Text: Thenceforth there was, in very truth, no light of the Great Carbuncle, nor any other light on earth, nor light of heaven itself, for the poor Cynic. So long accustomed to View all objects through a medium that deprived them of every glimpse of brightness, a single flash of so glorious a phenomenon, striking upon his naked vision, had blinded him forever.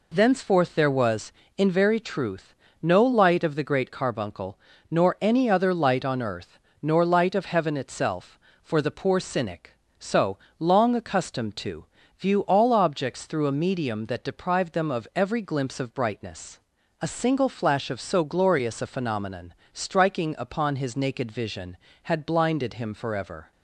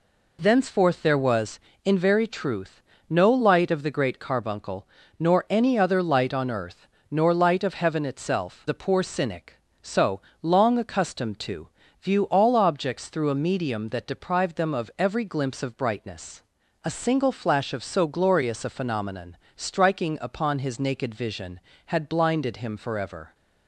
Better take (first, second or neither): first